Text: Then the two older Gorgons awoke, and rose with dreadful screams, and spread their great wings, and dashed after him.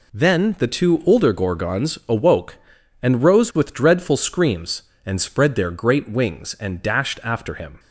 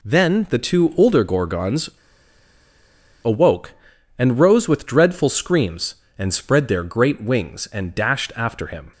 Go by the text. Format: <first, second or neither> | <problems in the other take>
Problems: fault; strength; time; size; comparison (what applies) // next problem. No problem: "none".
first | pauses between "Gorgons" and "awoke"; strong; at 1.9 s; 1.3 s long